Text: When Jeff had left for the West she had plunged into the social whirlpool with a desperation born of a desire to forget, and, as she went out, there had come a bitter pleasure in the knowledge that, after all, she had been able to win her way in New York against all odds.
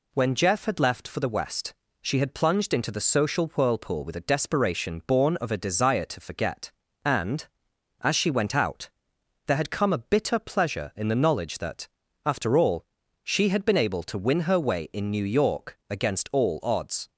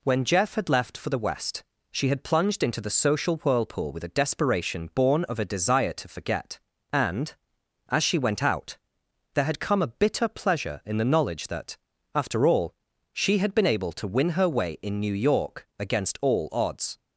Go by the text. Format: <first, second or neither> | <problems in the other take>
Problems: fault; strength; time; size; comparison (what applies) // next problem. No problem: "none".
neither | pauses between "West" and "she"; slight; the same in both